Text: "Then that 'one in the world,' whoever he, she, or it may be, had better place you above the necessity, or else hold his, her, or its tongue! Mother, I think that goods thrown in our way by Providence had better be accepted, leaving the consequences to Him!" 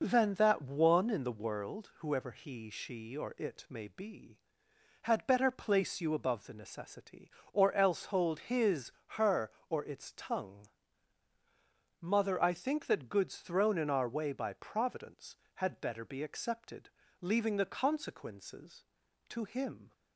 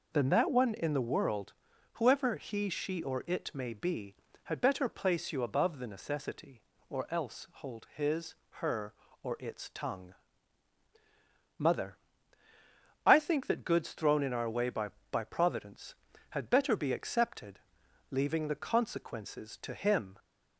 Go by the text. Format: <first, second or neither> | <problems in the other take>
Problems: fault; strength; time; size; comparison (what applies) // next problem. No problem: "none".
first | says "by" twice; at 15.1 s